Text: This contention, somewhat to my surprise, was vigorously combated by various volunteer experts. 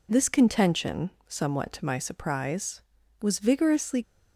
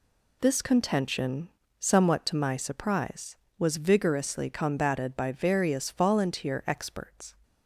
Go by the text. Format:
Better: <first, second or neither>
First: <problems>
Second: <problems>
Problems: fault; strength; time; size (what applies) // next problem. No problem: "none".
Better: second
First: stops before "combated by various volunteer experts"; at 4.0 s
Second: none